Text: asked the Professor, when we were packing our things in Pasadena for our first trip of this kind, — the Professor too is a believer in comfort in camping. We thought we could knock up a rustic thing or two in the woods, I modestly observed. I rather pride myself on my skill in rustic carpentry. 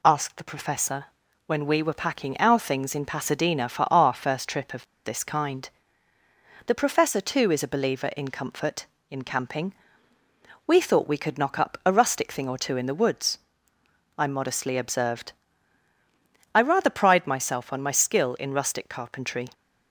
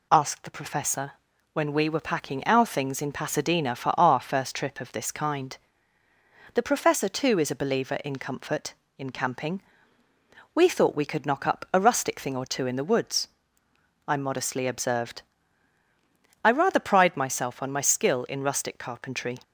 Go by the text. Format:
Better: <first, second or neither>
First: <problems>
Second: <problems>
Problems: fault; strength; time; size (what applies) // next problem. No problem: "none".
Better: second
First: pauses between "of" and "this"; slight; at 4.8 s; 0.19 s long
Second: none